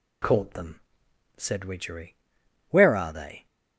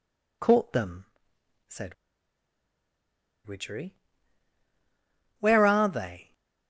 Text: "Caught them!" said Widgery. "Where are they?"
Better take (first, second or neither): first